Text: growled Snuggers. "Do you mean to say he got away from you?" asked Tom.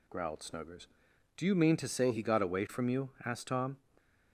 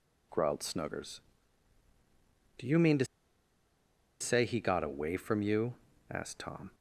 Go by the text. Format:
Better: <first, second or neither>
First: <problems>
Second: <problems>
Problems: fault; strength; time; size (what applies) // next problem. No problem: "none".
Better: first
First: none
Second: pauses between "to" and "say"; at 3.0 s; 1.1 s long